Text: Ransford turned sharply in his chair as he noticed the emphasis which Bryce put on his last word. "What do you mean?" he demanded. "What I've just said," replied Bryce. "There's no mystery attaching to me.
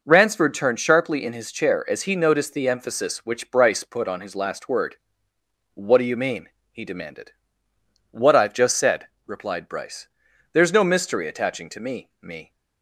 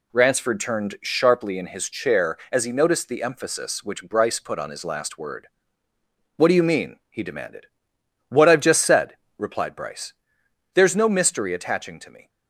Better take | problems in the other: second | says "me" twice; at 12.1 s

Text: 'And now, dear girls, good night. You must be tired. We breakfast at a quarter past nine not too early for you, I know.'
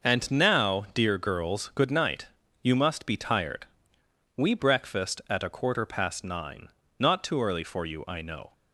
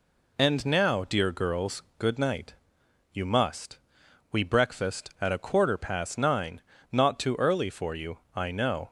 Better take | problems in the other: first | skips "be tired"; at 4.0 s // pauses between "nine" and "not"; slight; at 6.5 s; 0.32 s long; slight in the first

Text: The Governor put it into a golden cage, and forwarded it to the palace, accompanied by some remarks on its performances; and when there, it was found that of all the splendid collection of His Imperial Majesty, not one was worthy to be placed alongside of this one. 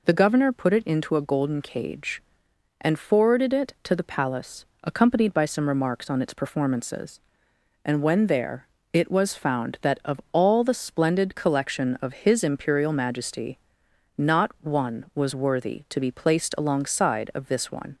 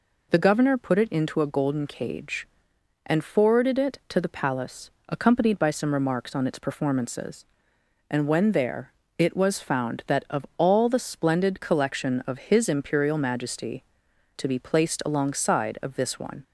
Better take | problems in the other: first | skips "not one was worthy"; at 14.0 s

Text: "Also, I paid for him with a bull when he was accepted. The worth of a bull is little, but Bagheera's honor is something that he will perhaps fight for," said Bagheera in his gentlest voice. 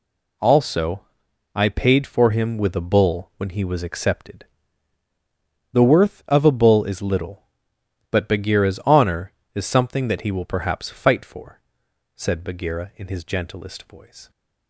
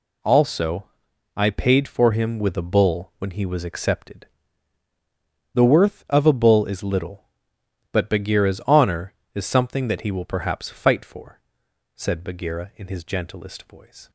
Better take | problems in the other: neither | none

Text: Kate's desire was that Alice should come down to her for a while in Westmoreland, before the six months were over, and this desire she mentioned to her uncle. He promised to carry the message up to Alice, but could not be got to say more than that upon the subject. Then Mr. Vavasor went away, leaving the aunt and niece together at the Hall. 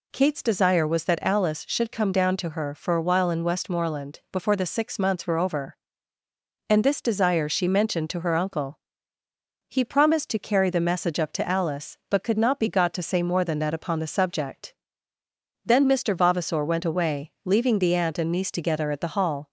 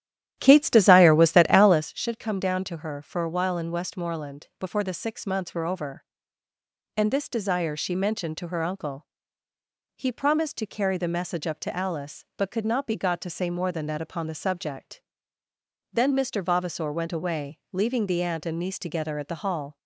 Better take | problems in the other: first | starts louder than the rest; strong; until 1.9 s; 11.5 dB

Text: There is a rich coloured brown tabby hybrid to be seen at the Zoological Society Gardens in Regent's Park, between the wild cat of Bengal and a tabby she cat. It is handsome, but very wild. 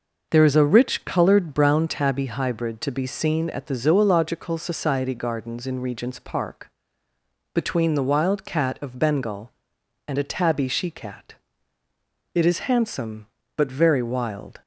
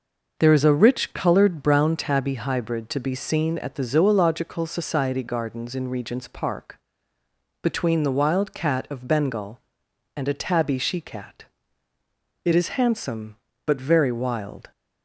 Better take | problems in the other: neither | none

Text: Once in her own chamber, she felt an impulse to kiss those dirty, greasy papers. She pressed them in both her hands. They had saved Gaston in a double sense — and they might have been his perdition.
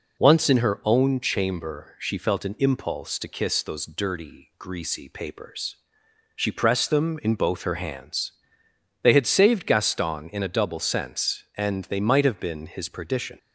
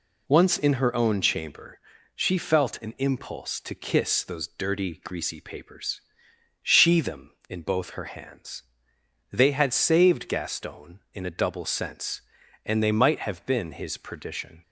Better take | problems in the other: first | skips "pressed"; at 7.0 s

